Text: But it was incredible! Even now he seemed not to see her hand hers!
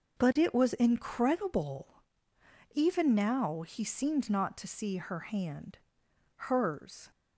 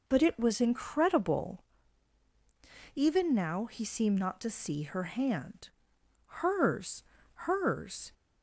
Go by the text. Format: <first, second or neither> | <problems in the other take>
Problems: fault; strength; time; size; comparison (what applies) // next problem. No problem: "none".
first | pauses between "hand" and "hers"; noticeable; at 5.6 s; 0.72 s long; noticeable in the first // says "hers" twice; at 7.4 s